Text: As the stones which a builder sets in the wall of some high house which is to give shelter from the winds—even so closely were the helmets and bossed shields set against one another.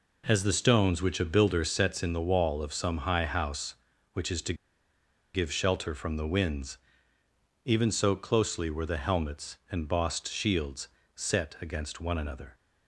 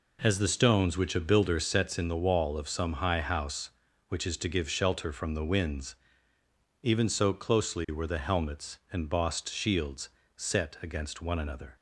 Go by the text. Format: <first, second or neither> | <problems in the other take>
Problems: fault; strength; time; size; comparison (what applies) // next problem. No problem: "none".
second | pauses between "to" and "give"; noticeable; at 4.5 s; 0.79 s long // pauses between "shields" and "set"; slight; at 10.8 s; 0.30 s long; slight in the second